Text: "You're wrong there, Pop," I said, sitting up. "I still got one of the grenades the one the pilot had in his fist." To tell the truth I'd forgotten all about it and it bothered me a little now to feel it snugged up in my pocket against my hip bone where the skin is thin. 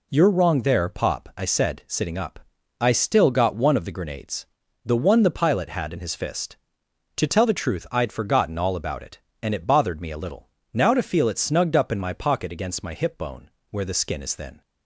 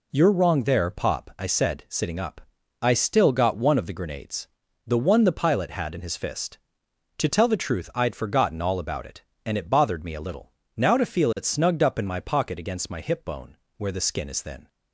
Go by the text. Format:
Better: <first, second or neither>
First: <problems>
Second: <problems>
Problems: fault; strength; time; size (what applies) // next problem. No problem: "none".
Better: neither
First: pauses between "grenades" and "the"; slight; at 4.4 s; 0.36 s long // pauses between "little" and "now"; slight; at 10.4 s; 0.24 s long // pauses between "bone" and "where"; slight; at 13.5 s; 0.20 s long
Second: pauses between "grenades" and "the"; slight; at 4.4 s; 0.36 s long // pauses between "little" and "now"; slight; at 10.5 s; 0.24 s long // pauses between "bone" and "where"; slight; at 13.5 s; 0.20 s long